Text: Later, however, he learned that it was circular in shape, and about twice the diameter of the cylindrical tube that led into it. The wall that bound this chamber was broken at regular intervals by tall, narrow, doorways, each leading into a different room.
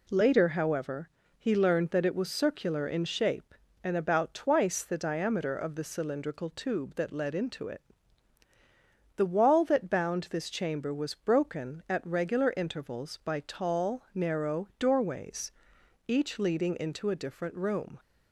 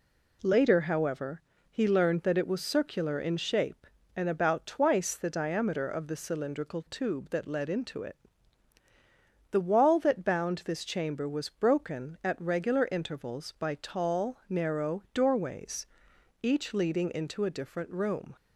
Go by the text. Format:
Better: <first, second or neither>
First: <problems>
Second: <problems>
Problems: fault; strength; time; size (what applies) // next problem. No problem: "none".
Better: neither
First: none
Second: none